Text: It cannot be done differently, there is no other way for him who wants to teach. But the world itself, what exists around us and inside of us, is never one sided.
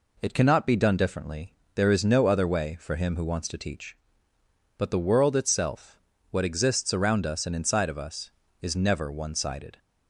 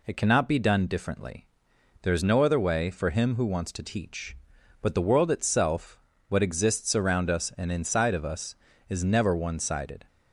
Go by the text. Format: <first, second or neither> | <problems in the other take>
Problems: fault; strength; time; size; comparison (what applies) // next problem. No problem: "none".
neither | none